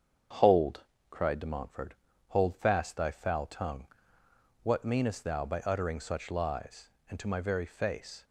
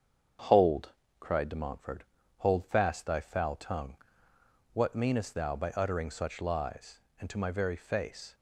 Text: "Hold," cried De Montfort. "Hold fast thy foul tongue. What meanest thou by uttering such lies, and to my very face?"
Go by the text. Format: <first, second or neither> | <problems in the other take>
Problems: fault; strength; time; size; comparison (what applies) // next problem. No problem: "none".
neither | starts louder than the rest; strong; the same in both